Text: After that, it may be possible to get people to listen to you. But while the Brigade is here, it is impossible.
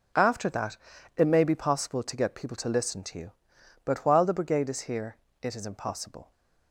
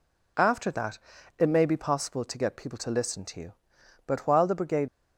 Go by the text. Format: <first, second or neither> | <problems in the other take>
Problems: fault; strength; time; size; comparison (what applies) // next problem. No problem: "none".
first | stops before "is here it is impossible"; at 4.8 s